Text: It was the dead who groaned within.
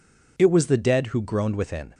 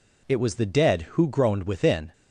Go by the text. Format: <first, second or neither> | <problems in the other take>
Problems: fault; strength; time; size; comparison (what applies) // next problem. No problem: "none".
neither | none